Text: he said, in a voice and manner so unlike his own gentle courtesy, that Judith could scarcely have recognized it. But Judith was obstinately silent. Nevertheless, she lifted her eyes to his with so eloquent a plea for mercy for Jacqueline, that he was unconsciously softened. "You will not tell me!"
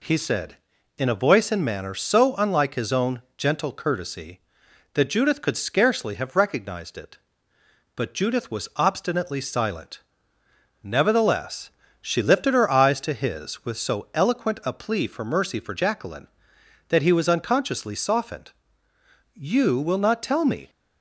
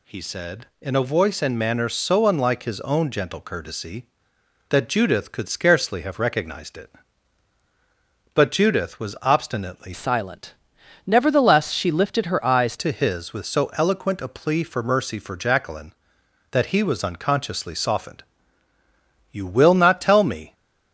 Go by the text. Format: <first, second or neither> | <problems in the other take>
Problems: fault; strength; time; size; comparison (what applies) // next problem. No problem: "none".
first | changes voice from "silent" to "eyes"; from 9.9 to 12.7 s; 2.8 s long